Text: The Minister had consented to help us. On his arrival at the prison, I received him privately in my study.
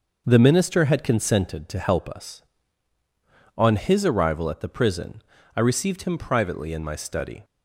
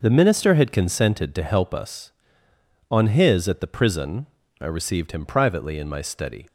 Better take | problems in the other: first | skips "arrival"; at 3.4 s

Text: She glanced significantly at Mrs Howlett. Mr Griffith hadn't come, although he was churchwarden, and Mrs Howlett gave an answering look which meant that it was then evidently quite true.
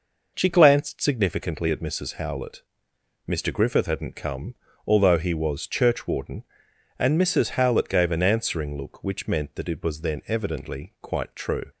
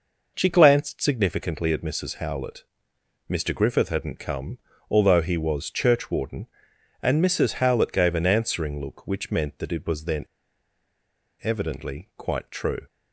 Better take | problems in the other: first | pauses between "then" and "evidently"; at 10.2 s; 1.1 s long

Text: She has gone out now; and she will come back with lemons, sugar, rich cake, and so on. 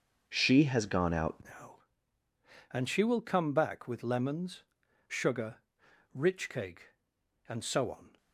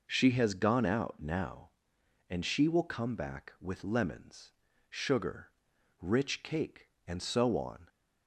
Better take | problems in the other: second | starts louder than the rest; until 1.2 s; 6.5 dB // changes voice at "now"; from 1.4 s on; 6.7 s long

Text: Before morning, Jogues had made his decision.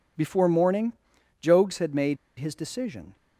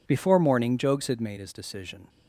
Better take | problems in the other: second | pauses between "made" and "his"; slight; at 2.1 s; 0.22 s long

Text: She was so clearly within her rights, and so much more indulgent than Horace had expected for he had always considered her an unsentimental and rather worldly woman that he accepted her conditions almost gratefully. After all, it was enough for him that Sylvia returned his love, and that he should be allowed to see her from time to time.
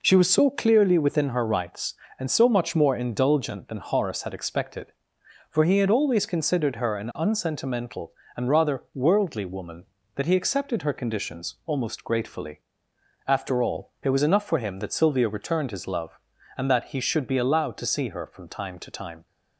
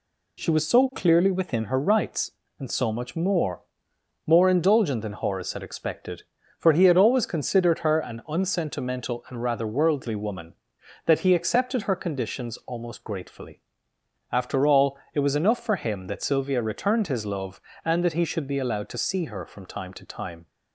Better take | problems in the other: first | says "more" twice; at 4.2 s

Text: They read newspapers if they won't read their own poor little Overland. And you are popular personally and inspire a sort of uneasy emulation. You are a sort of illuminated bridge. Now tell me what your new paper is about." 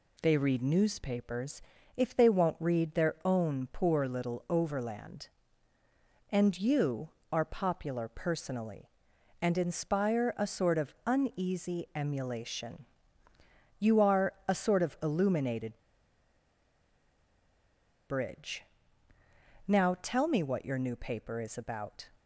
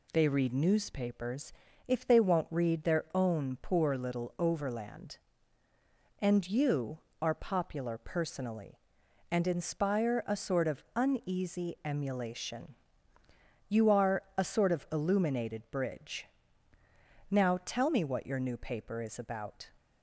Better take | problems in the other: second | pauses between "newspapers" and "if"; slight; at 1.6 s; 0.34 s long; slight in the second // pauses between "illuminated" and "bridge"; strong; at 15.7 s; 2.3 s long

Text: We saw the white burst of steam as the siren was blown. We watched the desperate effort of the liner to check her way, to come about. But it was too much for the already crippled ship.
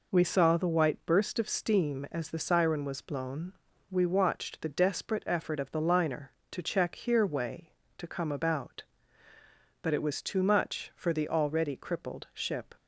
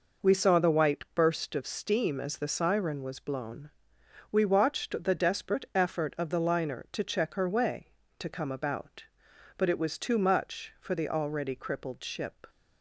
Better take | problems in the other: second | says "here" for "her"; at 6.9 s

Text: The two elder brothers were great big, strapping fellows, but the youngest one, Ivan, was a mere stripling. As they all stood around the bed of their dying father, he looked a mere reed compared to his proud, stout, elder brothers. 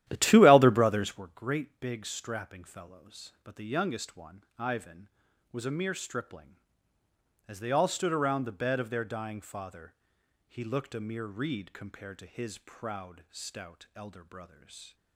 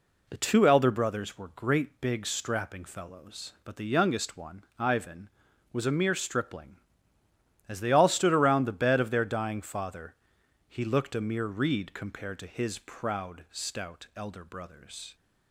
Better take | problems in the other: second | starts louder than the rest; strong; until 1.3 s; 12.5 dB

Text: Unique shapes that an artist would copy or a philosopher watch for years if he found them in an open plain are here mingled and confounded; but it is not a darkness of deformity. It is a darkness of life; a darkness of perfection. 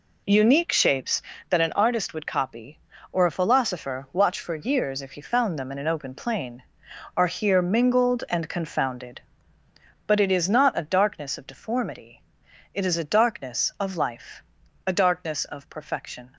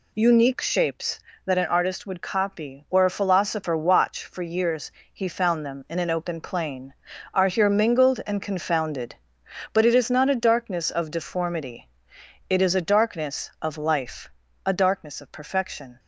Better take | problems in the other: first | skips "if"; at 5.0 s

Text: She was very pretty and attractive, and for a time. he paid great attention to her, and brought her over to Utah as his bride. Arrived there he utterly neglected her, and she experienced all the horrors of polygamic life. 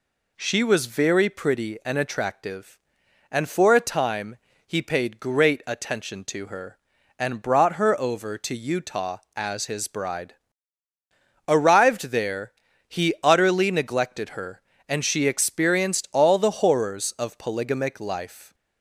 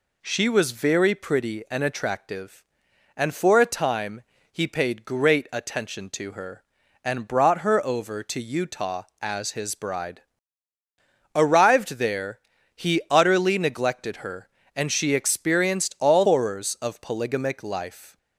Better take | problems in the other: first | pauses between "there" and "he"; slight; at 12.3 s; 0.36 s long; slight in the first // skips "the"; at 16.2 s

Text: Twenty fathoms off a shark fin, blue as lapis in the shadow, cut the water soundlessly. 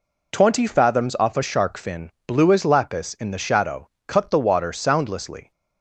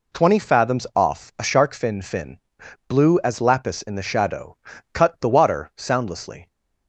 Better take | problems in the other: first | says "fin" twice; at 2.0 s

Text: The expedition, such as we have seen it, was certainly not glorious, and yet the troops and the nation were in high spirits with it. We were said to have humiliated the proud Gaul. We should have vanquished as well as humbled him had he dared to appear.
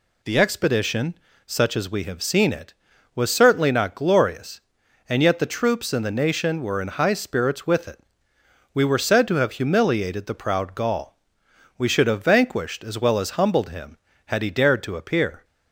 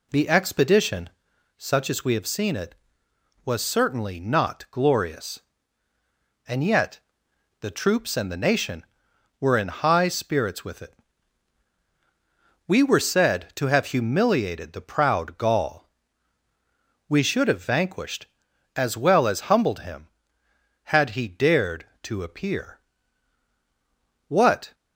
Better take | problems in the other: first | pauses between "yet" and "the"; noticeable; at 6.9 s; 0.60 s long // goes on to say "What"; slight; from 24.2 s on; 0.46 s long

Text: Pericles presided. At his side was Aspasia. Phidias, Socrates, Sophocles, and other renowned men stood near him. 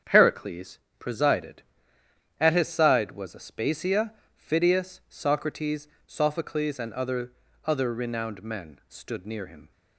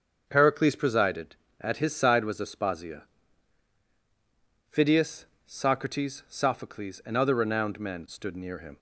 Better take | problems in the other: second | starts louder than the rest; strong; until 1.2 s; 7.5 dB; also in the second // pauses between "Pericles" and "presided"; slight; at 0.7 s; 0.20 s long // says "other" twice; at 7.6 s

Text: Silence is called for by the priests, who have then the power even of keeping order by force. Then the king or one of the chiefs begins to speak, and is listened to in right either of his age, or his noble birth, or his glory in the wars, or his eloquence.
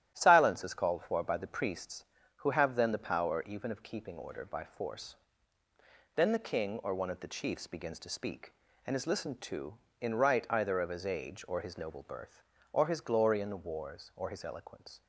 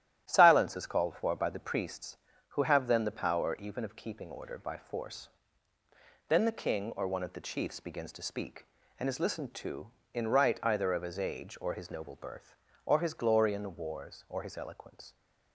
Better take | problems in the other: neither | starts louder than the rest; strong; the same in both

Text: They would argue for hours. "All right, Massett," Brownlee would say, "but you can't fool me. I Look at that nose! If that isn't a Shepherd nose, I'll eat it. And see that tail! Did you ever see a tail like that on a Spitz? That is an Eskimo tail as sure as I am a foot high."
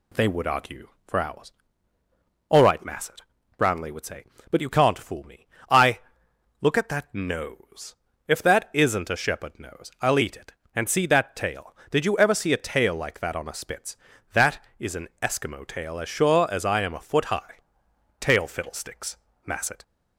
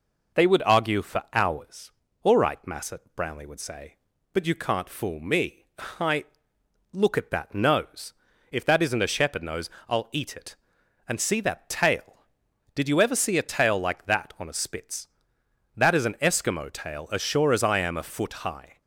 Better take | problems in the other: second | pauses between "I" and "Look"; noticeable; at 6.0 s; 0.60 s long; noticeable in the second // goes on to say "Tail fiddlesticks Massett"; from 18.2 s on; 1.6 s long

